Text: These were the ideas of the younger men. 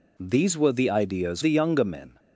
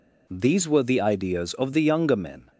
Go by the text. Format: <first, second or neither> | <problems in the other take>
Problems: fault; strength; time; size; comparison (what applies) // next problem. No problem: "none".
second | skips "of"; at 1.4 s